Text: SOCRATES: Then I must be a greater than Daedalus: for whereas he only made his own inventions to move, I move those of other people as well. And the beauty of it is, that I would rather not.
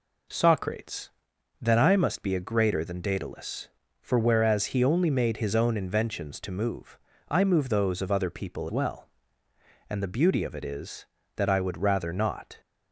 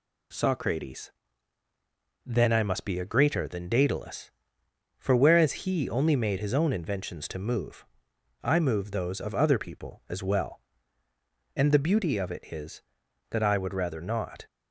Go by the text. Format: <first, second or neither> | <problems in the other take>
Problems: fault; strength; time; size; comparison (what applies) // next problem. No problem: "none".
second | skips "as"; at 8.6 s